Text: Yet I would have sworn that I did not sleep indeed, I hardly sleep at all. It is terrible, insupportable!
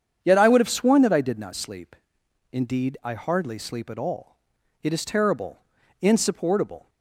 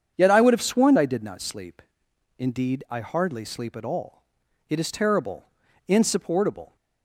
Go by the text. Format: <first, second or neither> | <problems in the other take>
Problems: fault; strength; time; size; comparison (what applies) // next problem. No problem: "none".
first | starts louder than the rest; strong; until 1.2 s; 7.5 dB; strong in the first // skips "that"; at 0.9 s // pauses between "sleep" and "indeed"; noticeable; at 1.8 s; 0.56 s long; noticeable in the first